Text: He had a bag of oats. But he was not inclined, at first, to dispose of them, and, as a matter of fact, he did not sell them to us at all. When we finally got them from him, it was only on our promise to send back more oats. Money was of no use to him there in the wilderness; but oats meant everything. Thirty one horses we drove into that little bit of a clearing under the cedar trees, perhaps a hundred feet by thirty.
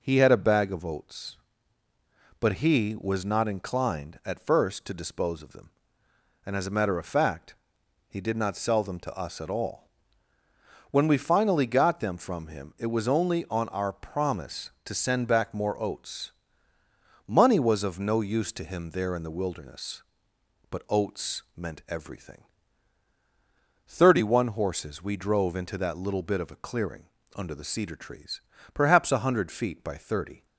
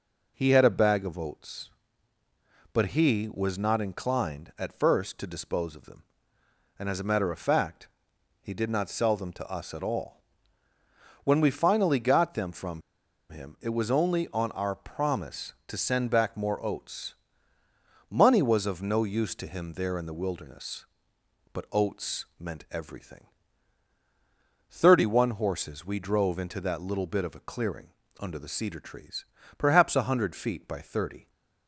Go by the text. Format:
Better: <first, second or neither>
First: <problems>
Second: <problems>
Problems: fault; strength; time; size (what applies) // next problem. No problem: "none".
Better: first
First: pauses between "clearing" and "under"; slight; at 27.0 s; 0.32 s long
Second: pauses between "from" and "him"; noticeable; at 12.8 s; 0.48 s long // pauses between "clearing" and "under"; slight; at 27.8 s; 0.32 s long